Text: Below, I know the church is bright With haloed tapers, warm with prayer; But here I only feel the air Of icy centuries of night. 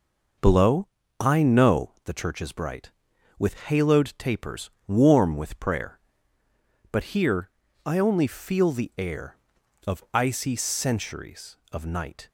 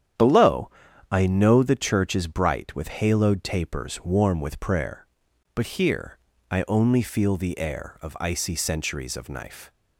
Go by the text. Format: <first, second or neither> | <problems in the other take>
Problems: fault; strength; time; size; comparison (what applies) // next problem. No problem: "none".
first | starts louder than the rest; strong; until 1.6 s; 9.5 dB // pauses between "here" and "I"; slight; at 6.1 s; 0.32 s long; slight in the first // says "knife" for "night"; at 9.2 s